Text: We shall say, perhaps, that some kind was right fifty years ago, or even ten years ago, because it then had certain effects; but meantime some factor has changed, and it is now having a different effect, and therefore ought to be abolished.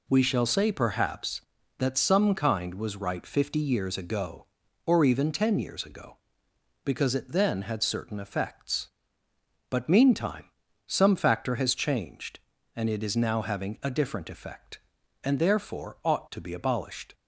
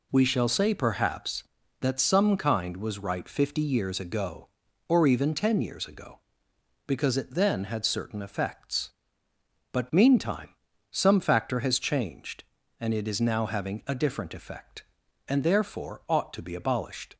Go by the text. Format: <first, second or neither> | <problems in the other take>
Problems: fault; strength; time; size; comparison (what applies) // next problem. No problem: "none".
neither | pauses between "meantime" and "some"; the same in both